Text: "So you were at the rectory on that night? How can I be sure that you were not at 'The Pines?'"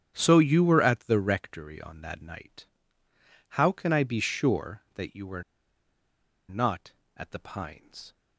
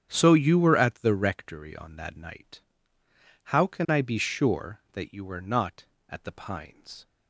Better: second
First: starts louder than the rest; strong; until 1.1 s; 9.5 dB // pauses between "were" and "not"; at 5.4 s; 1.0 s long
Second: starts louder than the rest; strong; until 1.1 s; 9.5 dB

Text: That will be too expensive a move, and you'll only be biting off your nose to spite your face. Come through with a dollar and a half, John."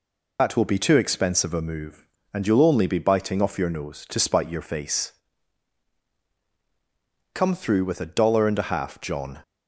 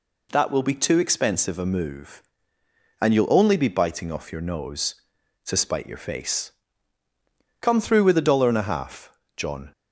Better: second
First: loses the start of "That"; at 0.3 s; 45 ms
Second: none

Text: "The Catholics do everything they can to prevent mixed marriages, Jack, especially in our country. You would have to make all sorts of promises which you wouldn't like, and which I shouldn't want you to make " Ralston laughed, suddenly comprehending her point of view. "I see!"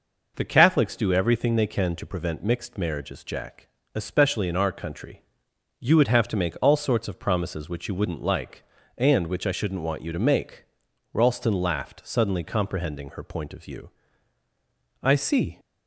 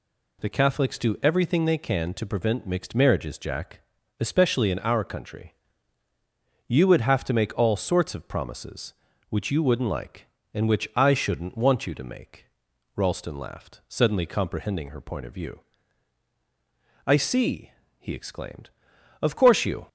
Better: first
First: none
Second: goes on to say "he exclaimed Of course you"; strong; from 17.9 s on; 1.9 s long

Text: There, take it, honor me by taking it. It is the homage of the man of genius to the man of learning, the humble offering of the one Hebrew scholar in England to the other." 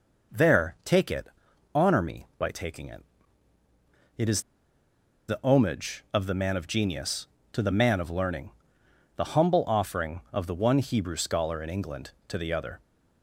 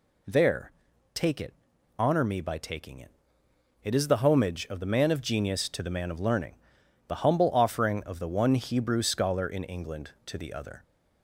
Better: second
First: pauses between "is" and "the"; noticeable; at 4.4 s; 0.87 s long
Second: none

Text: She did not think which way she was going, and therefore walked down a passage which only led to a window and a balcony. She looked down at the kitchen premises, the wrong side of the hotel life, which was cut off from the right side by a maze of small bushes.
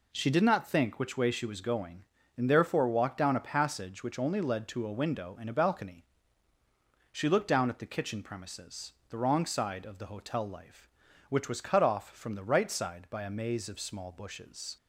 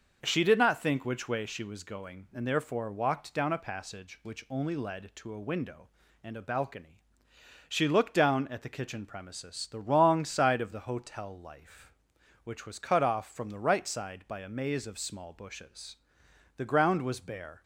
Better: first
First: none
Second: starts louder than the rest; until 1.2 s; 6 dB // goes on to say "The ground was bare"; noticeable; from 16.5 s on; 1.0 s long

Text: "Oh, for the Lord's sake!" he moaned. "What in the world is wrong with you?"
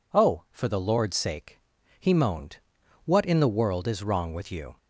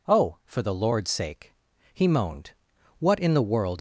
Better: first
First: none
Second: stops before "is wrong with you"; at 3.7 s

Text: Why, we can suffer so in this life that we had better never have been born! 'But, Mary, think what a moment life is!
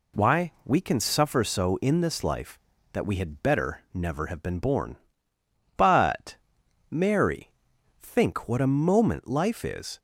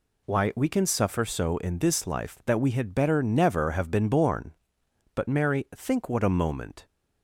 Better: first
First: none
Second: stops before "life is"; at 6.8 s

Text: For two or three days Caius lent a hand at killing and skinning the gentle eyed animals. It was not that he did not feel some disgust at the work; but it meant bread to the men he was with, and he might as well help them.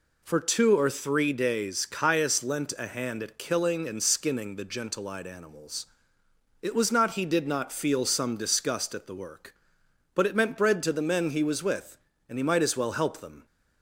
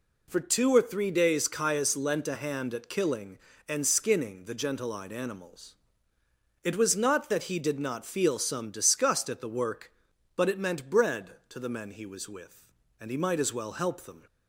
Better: second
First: skips "that"; at 7.1 s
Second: none

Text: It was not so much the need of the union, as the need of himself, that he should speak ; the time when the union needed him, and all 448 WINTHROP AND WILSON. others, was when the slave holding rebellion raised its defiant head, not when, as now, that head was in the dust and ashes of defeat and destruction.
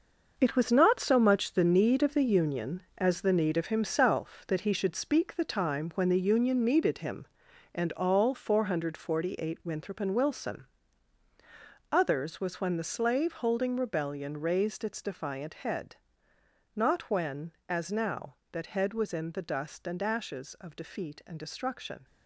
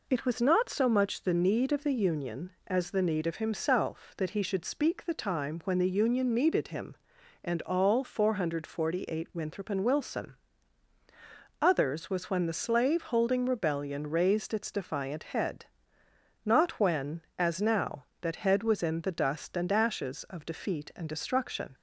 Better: second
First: gets quieter; strong; throughout; 10.5 dB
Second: none

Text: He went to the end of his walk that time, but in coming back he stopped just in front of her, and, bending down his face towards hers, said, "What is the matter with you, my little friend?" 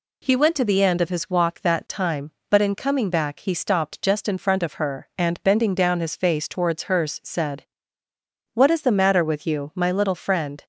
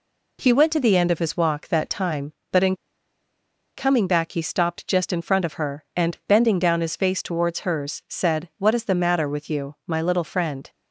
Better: first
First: none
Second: pauses between "in" and "coming"; at 2.7 s; 1.0 s long

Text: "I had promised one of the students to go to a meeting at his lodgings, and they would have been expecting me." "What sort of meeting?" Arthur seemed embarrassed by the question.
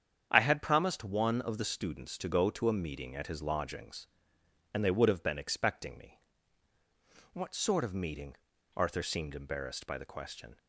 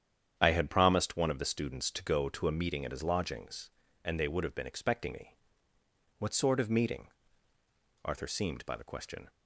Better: first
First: starts louder than the rest; strong; until 1.3 s; 8 dB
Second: starts louder than the rest; strong; until 1.3 s; 9 dB // skips "embarrassed"; at 8.6 s

